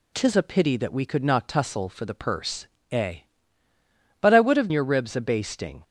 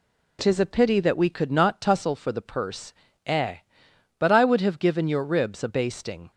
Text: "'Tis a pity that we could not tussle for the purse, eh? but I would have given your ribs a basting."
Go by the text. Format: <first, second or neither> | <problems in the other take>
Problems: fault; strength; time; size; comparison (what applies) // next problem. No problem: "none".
second | skips "given"; at 4.6 s